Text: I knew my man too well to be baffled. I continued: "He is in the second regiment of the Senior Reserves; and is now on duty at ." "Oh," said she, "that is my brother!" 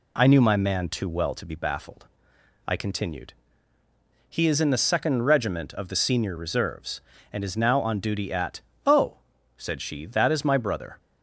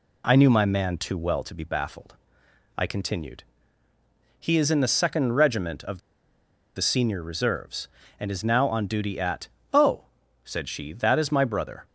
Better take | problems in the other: first | pauses between "of" and "the"; noticeable; at 5.9 s; 0.76 s long

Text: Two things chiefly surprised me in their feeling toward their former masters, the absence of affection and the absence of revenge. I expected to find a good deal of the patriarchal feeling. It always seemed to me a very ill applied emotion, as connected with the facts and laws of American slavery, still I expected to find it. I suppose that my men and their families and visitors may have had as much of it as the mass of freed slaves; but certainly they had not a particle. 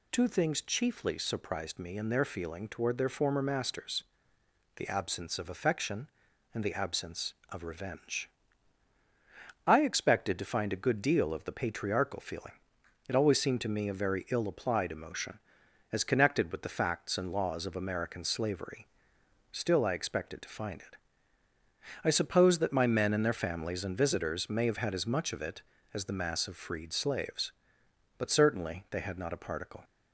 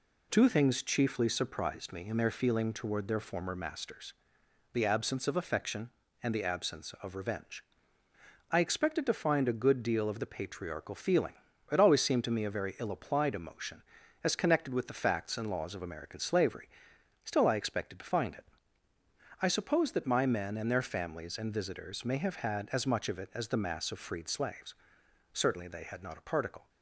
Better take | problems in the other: first | skips "but"; at 25.0 s

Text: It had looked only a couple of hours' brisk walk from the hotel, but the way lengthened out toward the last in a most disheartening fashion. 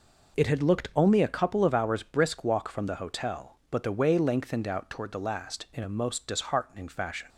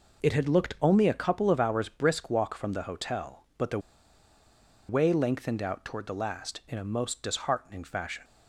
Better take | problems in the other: first | pauses between "the" and "way"; at 3.7 s; 1.1 s long

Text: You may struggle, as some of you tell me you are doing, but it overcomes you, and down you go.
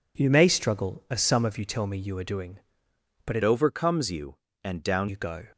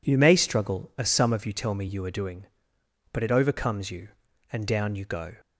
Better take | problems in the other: second | changes voice from "overcomes" to "down"; from 3.4 to 5.0 s; 1.6 s long

